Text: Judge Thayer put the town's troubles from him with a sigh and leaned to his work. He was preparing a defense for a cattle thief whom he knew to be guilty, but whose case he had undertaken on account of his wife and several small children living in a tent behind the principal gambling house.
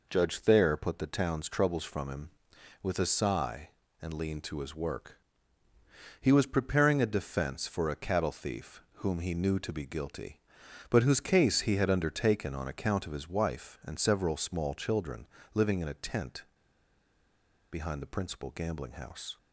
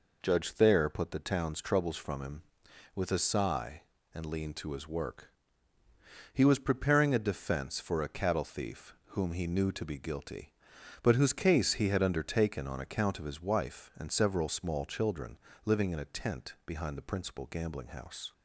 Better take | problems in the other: second | pauses between "thief" and "whom"; slight; at 8.7 s; 0.16 s long; slight in the second // pauses between "children" and "living"; slight; at 15.2 s; 0.28 s long; slight in the second // pauses between "tent" and "behind"; strong; at 16.4 s; 1.2 s long

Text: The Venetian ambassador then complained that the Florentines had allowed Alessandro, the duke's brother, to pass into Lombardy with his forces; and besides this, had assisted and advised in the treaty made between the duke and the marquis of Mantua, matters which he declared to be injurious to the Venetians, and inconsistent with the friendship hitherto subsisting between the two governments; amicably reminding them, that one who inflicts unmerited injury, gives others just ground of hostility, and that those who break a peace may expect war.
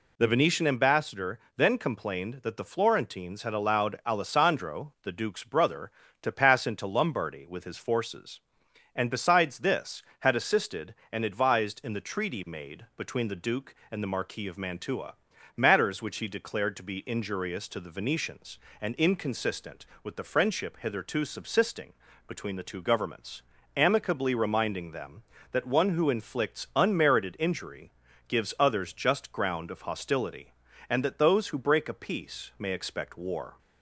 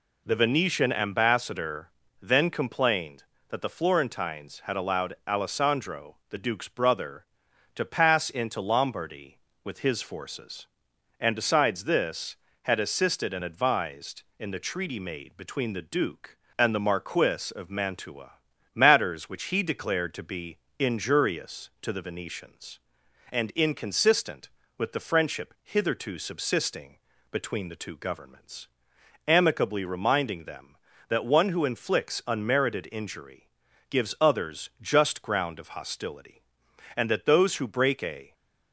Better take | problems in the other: first | pauses between "ambassador" and "then"; slight; at 1.8 s; 0.32 s long; slight in the first // pauses between "be" and "injurious"; slight; at 20.5 s; 0.18 s long // pauses between "subsisting" and "between"; slight; at 26.9 s; 0.34 s long; slight in the first // stops before "peace may expect war"; at 38.3 s

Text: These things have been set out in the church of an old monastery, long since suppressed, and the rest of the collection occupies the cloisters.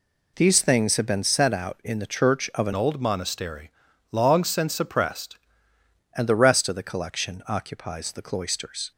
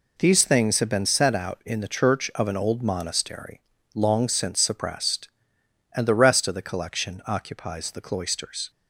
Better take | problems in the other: second | changes voice from "old" to "suppressed"; from 2.7 to 5.3 s; 2.6 s long

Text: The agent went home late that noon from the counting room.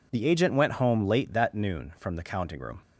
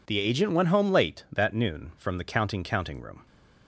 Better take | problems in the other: first | says "counting" twice; at 2.6 s

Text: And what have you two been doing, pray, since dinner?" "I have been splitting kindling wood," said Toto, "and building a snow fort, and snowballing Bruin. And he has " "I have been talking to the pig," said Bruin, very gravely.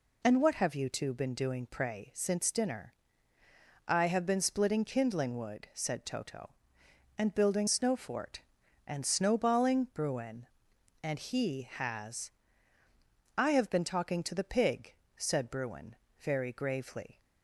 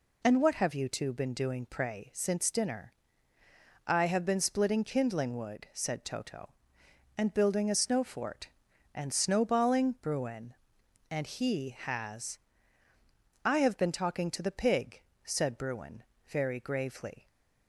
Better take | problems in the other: second | skips "a"; at 7.6 s

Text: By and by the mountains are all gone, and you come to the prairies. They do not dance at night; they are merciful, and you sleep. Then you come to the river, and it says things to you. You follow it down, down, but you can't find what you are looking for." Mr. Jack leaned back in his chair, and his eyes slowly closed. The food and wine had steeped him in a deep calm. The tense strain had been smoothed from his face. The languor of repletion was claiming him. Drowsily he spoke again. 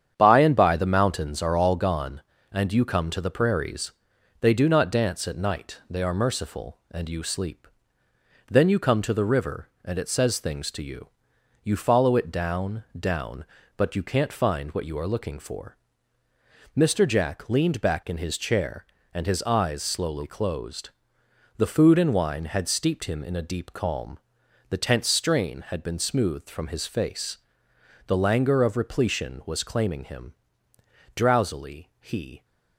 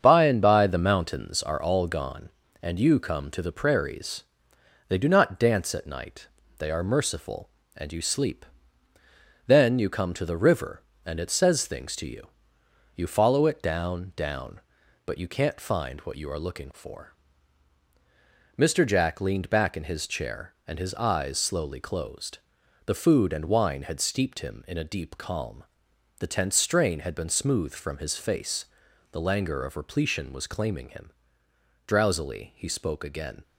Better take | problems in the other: second | starts louder than the rest; strong; until 1.1 s; 8.5 dB; strong in the second // stops before "spoke again"; at 32.4 s

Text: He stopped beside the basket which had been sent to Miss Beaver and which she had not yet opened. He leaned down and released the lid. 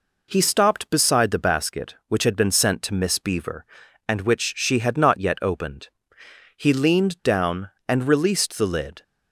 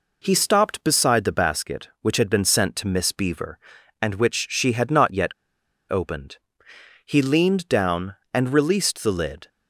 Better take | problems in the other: first | pauses between "yet" and "opened"; noticeable; at 5.3 s; 0.57 s long

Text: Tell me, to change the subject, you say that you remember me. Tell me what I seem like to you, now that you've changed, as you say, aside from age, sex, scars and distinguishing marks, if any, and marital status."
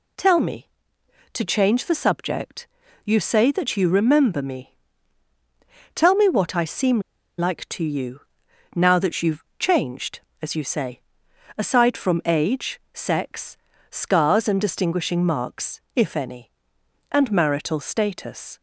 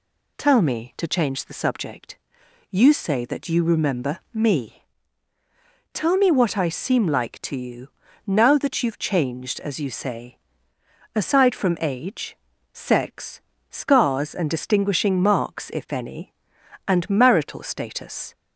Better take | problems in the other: second | pauses between "seem" and "like"; at 6.9 s; 0.38 s long // pauses between "you've" and "changed"; slight; at 9.4 s; 0.16 s long

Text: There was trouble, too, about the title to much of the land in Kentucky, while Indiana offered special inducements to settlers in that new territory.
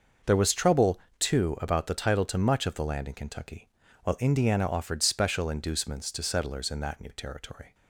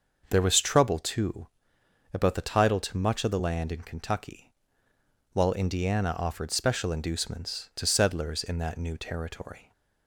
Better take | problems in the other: neither | starts louder than the rest; noticeable; the same in both

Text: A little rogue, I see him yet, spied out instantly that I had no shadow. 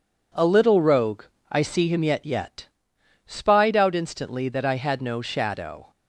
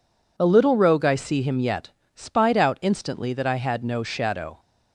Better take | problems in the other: second | says "yet" twice; at 2.2 s

